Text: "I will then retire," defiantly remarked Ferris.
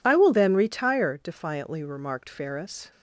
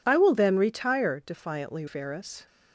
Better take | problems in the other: first | skips "remarked"; at 1.8 s

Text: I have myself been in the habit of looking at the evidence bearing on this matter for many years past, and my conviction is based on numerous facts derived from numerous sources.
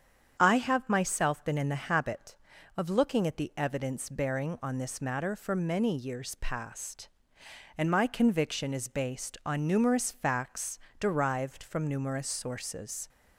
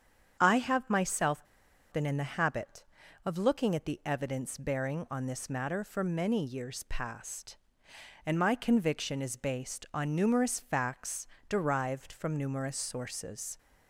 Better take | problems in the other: first | starts louder than the rest; strong; until 1.4 s; 8 dB; strong in the first // pauses between "myself" and "been"; noticeable; at 1.4 s; 0.49 s long // pauses between "facts" and "derived"; slight; at 11.2 s; 0.22 s long; slight in the first

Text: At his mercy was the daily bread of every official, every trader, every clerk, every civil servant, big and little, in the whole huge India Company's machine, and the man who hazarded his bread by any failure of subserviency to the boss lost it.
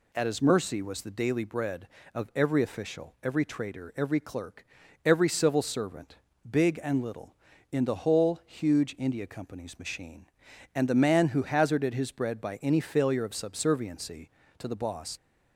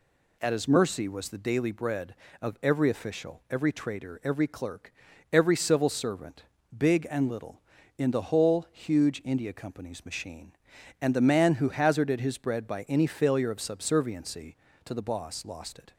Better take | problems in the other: second | stops before "lost it"; at 15.1 s

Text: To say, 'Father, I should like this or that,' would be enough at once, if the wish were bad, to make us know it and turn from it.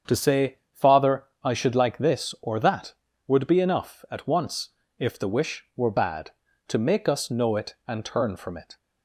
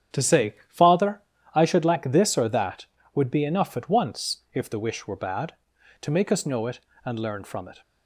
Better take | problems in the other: first | starts louder than the rest; strong; until 1.5 s; 9 dB; strong in the first // says "learn" for "turn"; at 7.1 s

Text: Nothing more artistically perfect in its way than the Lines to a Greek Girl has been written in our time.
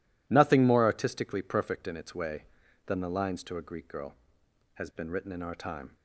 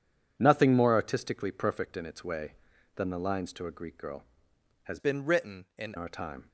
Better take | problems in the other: first | changes voice from "been" to "in"; from 4.9 to 5.9 s; 1.0 s long

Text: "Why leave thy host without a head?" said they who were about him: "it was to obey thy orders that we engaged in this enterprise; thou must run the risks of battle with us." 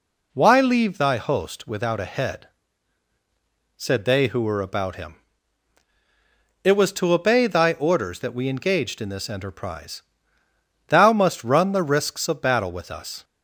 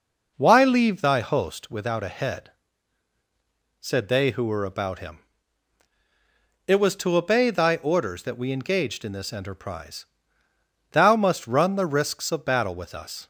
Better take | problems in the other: first | starts louder than the rest; noticeable; until 1.7 s; 5 dB

